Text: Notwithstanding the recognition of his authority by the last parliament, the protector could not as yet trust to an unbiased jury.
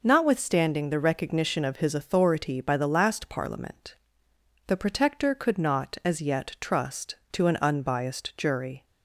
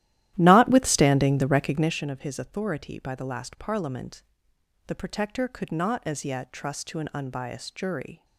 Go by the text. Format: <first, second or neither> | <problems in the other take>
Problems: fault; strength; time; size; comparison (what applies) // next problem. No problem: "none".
first | starts louder than the rest; strong; until 2.0 s; 13.5 dB